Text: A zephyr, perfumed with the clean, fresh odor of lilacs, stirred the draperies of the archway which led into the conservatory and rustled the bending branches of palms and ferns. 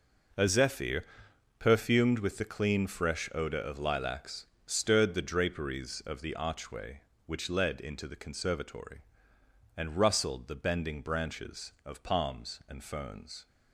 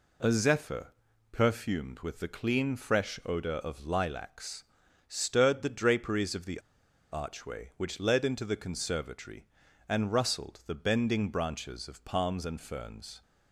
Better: first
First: none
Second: pauses between "the" and "archway"; noticeable; at 6.5 s; 0.52 s long

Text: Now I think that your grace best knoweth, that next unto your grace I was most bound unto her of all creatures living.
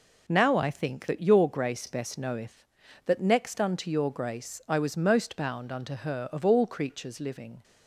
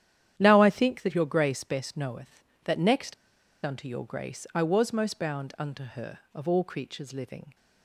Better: first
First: none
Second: starts louder than the rest; strong; until 1.3 s; 10.5 dB // pauses between "next" and "unto"; noticeable; at 3.1 s; 0.50 s long

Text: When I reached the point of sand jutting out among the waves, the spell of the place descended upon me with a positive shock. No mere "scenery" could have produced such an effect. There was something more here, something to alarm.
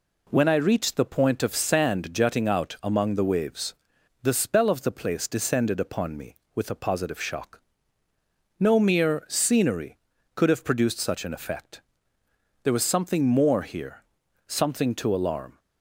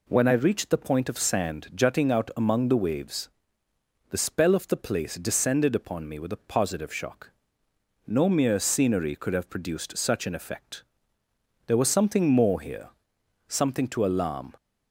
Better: neither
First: none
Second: none

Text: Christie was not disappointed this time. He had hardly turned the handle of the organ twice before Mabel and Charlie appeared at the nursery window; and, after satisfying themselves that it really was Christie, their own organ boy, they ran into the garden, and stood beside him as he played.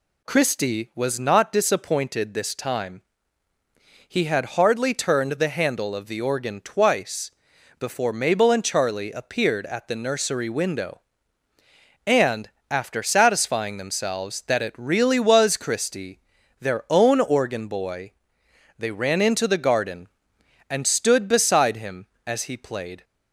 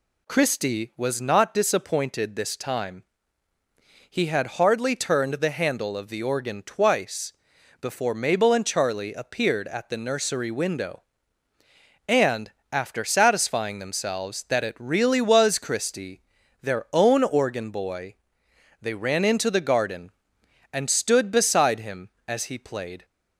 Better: neither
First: pauses between "twice" and "before"; noticeable; at 7.3 s; 0.48 s long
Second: pauses between "twice" and "before"; noticeable; at 7.3 s; 0.48 s long

